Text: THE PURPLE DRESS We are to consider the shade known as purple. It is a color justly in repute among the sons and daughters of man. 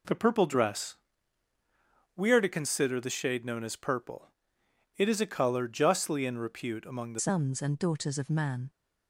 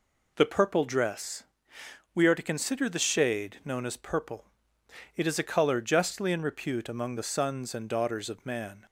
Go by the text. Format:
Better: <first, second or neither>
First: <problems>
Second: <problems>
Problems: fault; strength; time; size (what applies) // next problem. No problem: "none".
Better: second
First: pauses between "DRESS" and "We"; at 0.9 s; 1.2 s long // changes voice at "sons"; from 7.1 s on; 1.5 s long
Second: pauses between "DRESS" and "We"; noticeable; at 1.4 s; 0.72 s long